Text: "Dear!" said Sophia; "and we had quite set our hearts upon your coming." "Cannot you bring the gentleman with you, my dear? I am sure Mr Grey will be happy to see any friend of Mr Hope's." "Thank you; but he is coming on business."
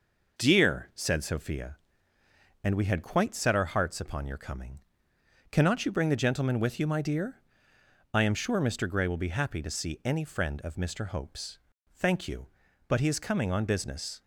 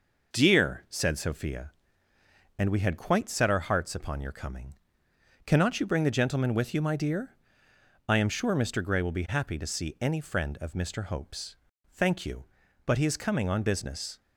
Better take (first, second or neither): neither